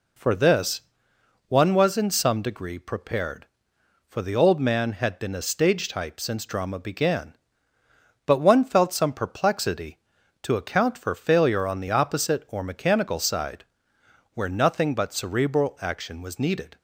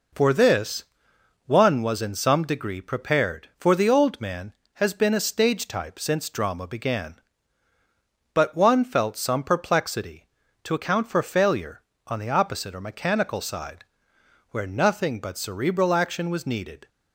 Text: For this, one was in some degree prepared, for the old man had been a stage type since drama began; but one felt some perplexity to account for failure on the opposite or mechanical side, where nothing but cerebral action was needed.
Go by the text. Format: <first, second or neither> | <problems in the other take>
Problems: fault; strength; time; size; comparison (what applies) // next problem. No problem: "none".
first | says "has" for "had"; at 4.7 s